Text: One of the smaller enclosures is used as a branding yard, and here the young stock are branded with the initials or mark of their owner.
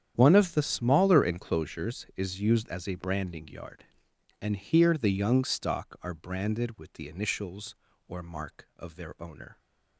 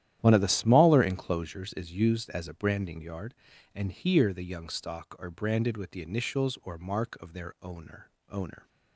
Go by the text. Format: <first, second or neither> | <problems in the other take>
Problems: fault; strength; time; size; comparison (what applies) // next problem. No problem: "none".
first | starts louder than the rest; strong; until 1.2 s; 11.5 dB; strong in the first // says "owner" twice; at 8.2 s